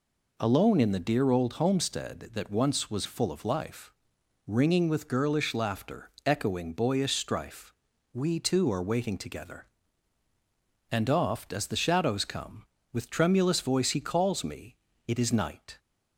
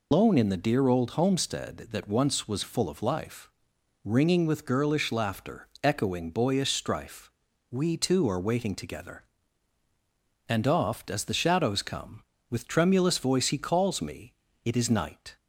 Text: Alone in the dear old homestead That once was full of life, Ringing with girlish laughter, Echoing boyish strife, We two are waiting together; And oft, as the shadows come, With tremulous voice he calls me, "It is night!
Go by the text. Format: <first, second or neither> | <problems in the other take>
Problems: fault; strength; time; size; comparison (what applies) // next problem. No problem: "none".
first | loses the start of "Alone"; at 0.1 s; 150 ms